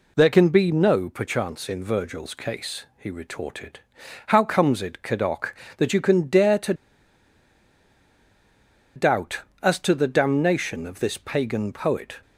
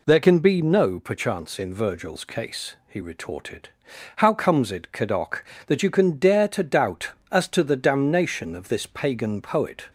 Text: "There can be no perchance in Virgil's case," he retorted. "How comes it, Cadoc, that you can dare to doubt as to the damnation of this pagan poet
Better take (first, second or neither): second